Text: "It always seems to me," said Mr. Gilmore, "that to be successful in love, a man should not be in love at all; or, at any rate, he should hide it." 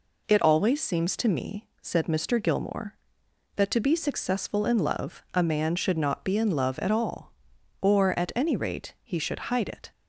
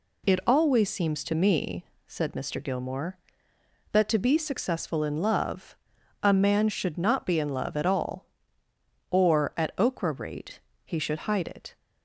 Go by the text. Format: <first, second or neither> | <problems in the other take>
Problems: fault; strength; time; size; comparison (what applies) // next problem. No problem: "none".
first | says "okra" for "any"; at 9.7 s